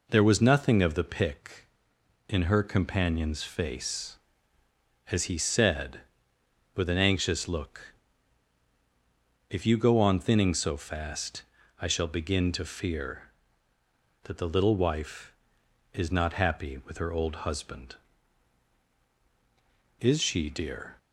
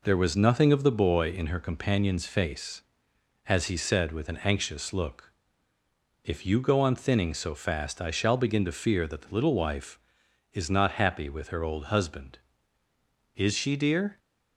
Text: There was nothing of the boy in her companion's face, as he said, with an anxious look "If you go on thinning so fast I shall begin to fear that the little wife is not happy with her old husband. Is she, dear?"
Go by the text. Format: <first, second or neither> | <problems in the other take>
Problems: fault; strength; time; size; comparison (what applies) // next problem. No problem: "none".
second | says "pick" for "boy"; at 1.0 s // pauses between "look" and "If"; strong; at 7.9 s; 1.5 s long; noticeable in the second // pauses between "fast" and "I"; at 11.4 s; 0.38 s long